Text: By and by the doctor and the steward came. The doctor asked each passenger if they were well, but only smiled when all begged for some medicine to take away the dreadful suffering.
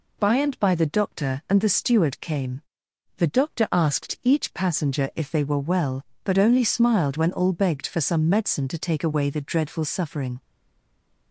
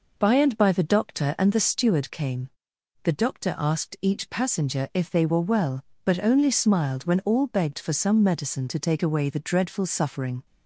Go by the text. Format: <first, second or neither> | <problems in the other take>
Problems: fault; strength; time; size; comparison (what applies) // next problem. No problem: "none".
second | stays silent after the last word; slight; from 10.3 s on; 1.0 s long